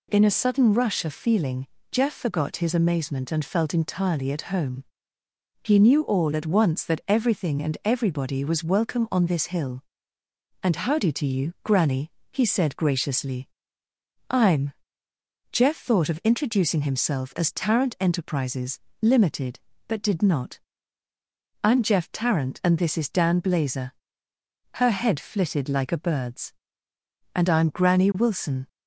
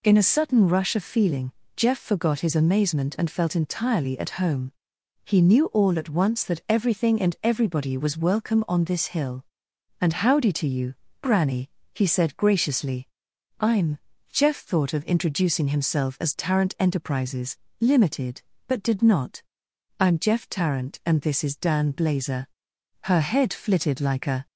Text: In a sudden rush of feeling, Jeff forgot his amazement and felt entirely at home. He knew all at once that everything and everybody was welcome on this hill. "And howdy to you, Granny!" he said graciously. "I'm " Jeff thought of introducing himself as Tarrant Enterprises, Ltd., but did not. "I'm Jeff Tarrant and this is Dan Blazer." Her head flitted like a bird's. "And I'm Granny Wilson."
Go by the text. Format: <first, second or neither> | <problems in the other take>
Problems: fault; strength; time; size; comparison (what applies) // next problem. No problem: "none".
first | stops before "bird's And I'm Granny Wilson"; at 24.4 s